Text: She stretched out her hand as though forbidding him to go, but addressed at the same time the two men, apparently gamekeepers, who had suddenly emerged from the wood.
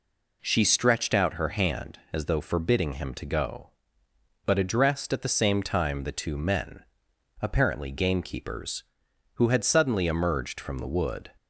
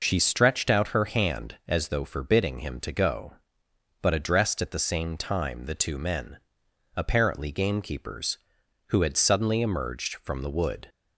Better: neither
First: none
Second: none

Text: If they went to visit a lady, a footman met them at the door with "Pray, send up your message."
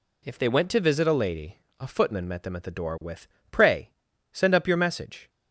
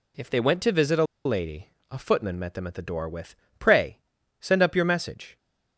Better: first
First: pauses between "with" and "Pray"; slight; at 3.2 s; 0.24 s long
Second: pauses between "a" and "lady"; slight; at 1.0 s; 0.21 s long // pauses between "with" and "Pray"; slight; at 3.3 s; 0.24 s long

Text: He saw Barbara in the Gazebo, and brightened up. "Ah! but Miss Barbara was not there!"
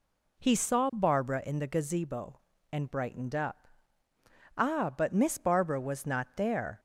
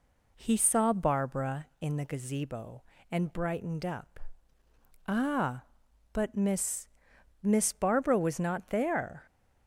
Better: first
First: none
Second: says "Miss" twice; at 7.4 s

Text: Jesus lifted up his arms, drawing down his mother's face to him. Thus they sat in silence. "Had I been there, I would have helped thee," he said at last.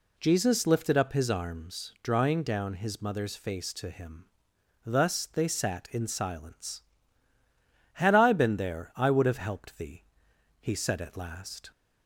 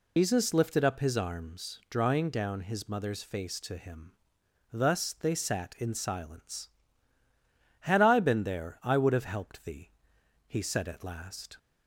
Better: first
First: none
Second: loses the start of "Jesus"; at 0.1 s; 105 ms

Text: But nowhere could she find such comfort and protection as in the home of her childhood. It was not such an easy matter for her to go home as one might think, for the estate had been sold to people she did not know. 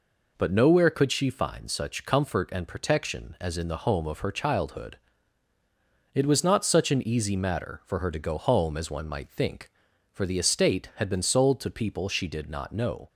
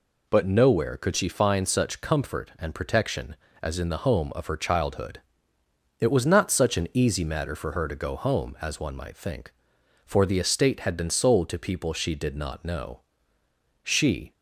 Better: first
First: none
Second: goes on to say "She"; from 13.8 s on; 0.50 s long

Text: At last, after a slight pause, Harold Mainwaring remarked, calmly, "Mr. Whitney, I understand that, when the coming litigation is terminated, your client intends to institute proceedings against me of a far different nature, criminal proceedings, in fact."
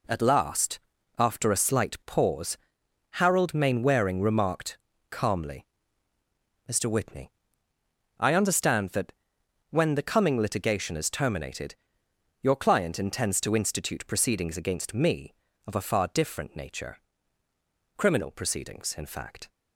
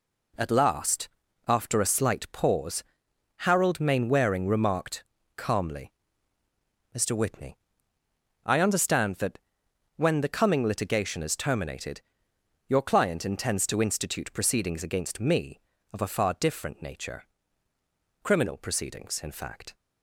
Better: neither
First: none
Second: none

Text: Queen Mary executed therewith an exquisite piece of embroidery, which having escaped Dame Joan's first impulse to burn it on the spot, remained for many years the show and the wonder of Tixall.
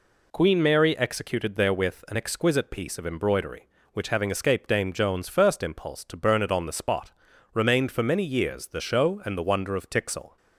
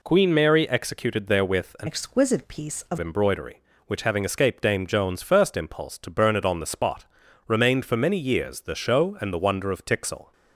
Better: first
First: none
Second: changes voice from "exquisite" to "of"; from 1.8 to 2.9 s; 1.1 s long

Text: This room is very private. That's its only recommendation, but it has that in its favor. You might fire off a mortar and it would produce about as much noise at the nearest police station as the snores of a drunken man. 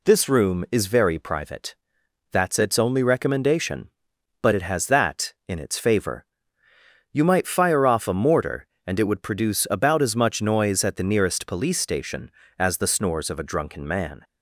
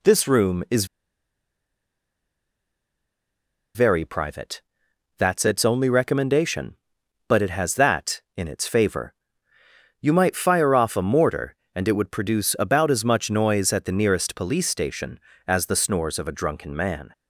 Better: first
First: none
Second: pauses between "is" and "very"; strong; at 0.8 s; 2.8 s long

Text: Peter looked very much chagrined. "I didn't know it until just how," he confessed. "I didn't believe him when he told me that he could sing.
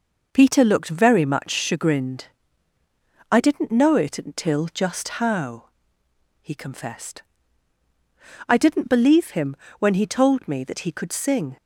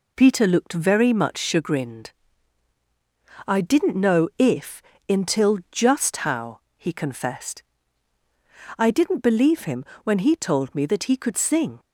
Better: first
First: pauses between "him" and "when"; slight; at 9.5 s; 0.22 s long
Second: says "if" for "it"; at 4.3 s // pauses between "him" and "when"; slight; at 9.8 s; 0.18 s long

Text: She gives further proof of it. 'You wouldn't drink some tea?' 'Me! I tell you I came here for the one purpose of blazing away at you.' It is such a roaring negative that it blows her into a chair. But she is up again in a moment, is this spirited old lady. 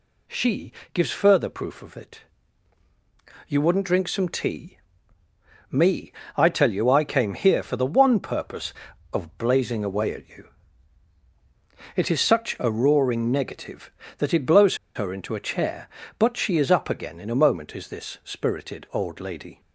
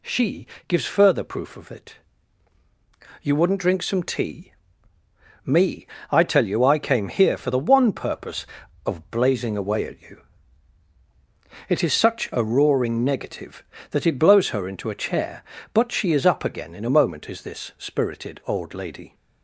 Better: second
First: pauses between "She" and "gives"; slight; at 0.7 s; 0.22 s long // pauses between "blows" and "her"; slight; at 14.7 s; 0.19 s long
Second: pauses between "She" and "gives"; slight; at 0.4 s; 0.22 s long

